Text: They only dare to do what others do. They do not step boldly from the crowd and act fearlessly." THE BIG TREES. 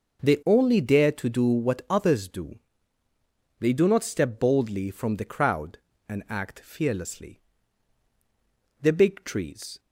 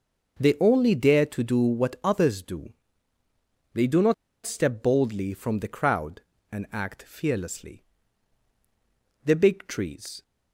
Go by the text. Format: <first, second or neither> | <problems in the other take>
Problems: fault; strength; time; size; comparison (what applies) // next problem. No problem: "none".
first | pauses between "not" and "step"; slight; at 4.1 s; 0.31 s long